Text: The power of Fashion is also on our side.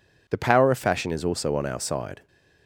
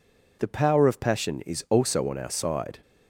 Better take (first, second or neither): first